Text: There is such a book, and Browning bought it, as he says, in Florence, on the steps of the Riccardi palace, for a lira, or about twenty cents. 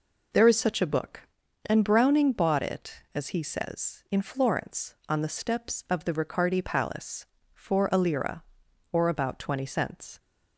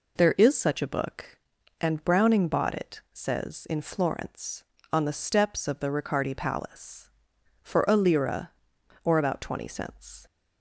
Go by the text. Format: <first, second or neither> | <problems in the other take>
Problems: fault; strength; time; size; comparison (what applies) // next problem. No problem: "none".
first | skips "as he"; at 3.0 s